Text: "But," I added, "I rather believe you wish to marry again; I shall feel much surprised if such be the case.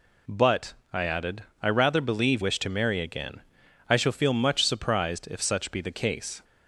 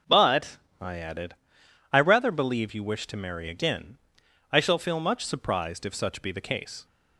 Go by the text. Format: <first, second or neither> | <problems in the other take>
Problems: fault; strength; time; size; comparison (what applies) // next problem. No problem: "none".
second | skips "you"; at 2.4 s